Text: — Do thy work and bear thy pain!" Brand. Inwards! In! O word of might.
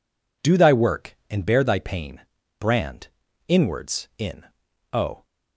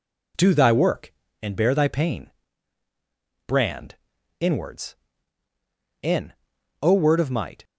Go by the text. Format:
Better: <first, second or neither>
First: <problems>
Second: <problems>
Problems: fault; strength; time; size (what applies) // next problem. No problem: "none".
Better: second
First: stops before "word of might"; at 5.2 s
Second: none